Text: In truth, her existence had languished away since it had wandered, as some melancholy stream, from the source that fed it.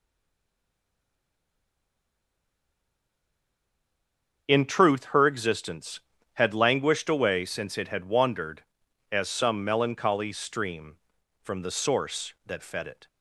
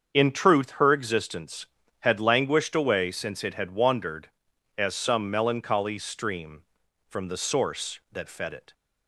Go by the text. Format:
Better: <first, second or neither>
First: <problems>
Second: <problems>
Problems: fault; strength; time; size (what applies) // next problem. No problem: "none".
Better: second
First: stays silent before the first word; strong; until 4.4 s; 4.4 s long // starts louder than the rest; until 5.4 s; 7 dB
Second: starts louder than the rest; until 1.1 s; 7 dB